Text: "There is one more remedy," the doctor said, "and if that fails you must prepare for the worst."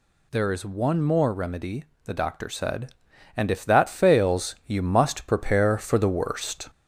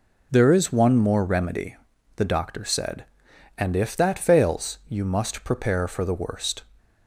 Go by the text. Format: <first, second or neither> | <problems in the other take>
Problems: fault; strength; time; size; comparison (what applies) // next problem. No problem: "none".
second | gets louder; slight; throughout; 2 dB